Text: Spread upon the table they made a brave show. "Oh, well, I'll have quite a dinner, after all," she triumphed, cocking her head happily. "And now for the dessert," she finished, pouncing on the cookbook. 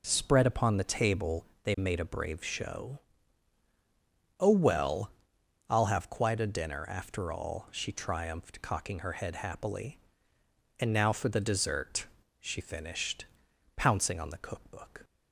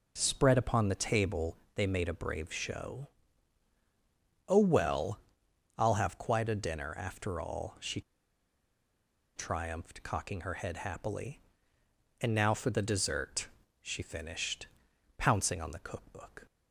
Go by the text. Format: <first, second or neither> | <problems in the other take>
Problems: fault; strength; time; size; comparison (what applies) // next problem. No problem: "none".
first | pauses between "table" and "they"; slight; at 1.5 s; 0.16 s long; slight in the first // pauses between "she" and "triumphed"; strong; at 8.0 s; 1.3 s long